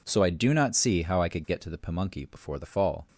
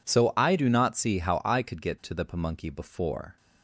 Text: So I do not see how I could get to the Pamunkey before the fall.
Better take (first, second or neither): first